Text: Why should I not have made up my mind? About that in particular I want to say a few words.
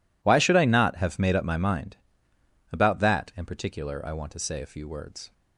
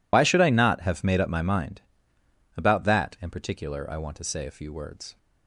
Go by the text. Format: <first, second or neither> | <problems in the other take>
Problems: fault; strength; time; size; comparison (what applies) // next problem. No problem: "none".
first | loses the start of "Why"; at 0.1 s; 55 ms